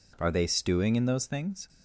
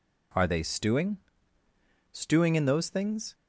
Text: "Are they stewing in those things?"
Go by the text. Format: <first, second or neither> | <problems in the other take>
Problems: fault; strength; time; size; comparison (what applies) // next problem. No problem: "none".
first | says "stewing" twice; at 2.1 s